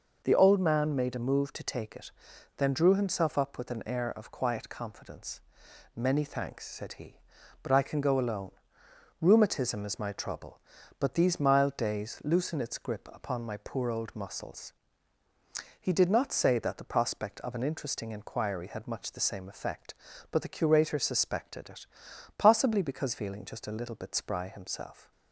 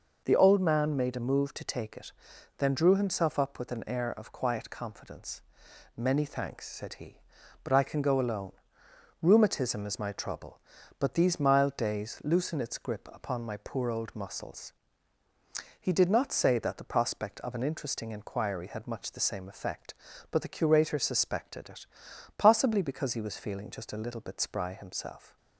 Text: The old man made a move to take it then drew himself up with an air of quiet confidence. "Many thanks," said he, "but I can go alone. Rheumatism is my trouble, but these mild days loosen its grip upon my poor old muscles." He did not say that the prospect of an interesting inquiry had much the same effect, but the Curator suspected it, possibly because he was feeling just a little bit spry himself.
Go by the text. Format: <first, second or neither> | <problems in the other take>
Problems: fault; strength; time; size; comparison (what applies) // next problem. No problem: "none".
second | pauses between "it" and "then"; noticeable; at 2.1 s; 0.46 s long; noticeable in the second // skips "he was"; at 23.1 s